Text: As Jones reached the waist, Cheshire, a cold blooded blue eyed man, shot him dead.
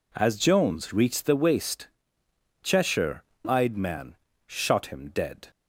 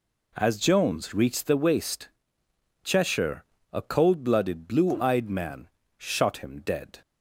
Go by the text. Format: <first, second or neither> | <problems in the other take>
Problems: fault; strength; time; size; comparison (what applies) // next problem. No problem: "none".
second | skips "a cold blooded blue"; at 3.3 s